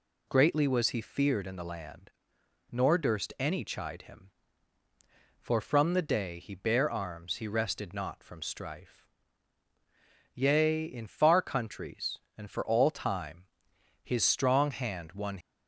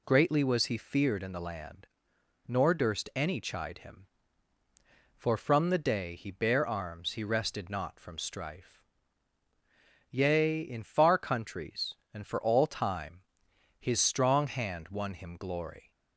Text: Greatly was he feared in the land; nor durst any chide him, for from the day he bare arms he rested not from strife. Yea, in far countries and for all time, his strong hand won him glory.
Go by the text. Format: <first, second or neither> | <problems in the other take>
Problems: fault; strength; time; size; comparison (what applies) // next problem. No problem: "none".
second | stops before "him glory"; at 15.4 s